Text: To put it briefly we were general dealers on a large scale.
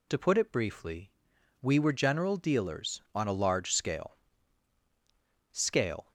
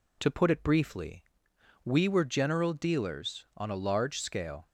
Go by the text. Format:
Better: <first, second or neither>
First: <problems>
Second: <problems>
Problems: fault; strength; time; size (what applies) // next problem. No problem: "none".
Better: second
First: pauses between "briefly" and "we"; noticeable; at 1.0 s; 0.54 s long // says "scale" twice; at 5.5 s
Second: pauses between "briefly" and "we"; noticeable; at 1.2 s; 0.62 s long